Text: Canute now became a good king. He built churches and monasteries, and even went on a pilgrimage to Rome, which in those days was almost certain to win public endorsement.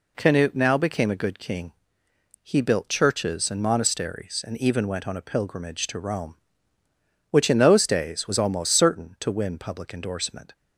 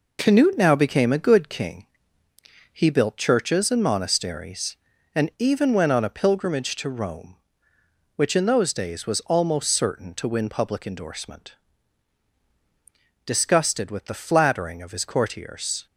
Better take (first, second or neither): first